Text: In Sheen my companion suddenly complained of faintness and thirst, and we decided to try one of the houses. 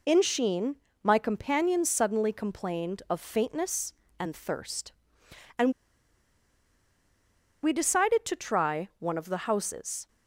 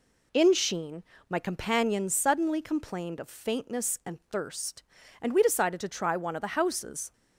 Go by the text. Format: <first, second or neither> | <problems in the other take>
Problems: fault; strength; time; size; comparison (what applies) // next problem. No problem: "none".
second | pauses between "Sheen" and "my"; slight; at 0.7 s; 0.26 s long; slight in the second // pauses between "and" and "we"; strong; at 5.7 s; 1.9 s long